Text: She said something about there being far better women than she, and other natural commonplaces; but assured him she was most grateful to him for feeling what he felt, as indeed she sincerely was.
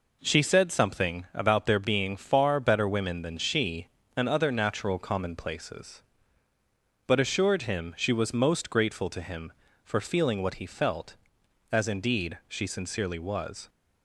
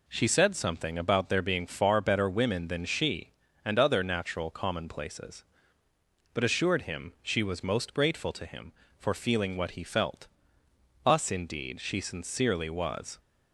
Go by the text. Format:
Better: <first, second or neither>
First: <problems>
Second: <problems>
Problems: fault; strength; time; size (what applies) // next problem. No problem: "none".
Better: first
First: none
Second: says "us" for "as"; at 11.0 s